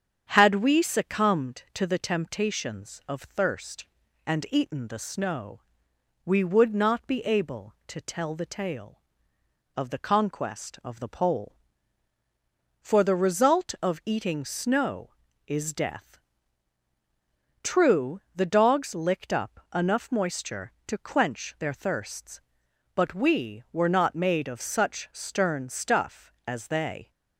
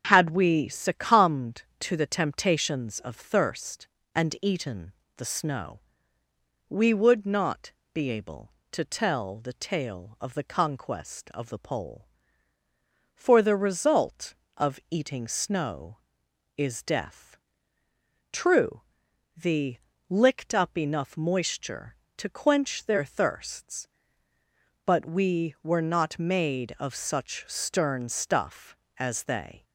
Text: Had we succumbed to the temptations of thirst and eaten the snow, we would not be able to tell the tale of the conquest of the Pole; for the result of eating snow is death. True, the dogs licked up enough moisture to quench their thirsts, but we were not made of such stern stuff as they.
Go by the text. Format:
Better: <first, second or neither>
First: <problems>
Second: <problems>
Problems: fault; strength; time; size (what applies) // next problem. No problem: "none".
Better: first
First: starts louder than the rest; strong; until 1.2 s; 8 dB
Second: starts louder than the rest; until 1.0 s; 7 dB // pauses between "eaten" and "the"; slight; at 4.9 s; 0.24 s long // pauses between "not" and "be"; slight; at 7.7 s; 0.20 s long // skips "dogs"; at 19.9 s